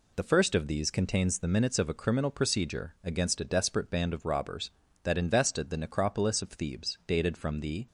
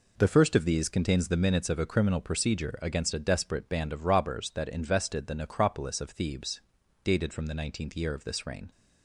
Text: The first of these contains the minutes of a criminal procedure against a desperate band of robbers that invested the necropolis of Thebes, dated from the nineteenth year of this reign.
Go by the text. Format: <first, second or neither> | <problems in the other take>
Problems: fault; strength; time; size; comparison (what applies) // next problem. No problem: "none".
second | stops before "nineteenth year of this reign"; at 7.8 s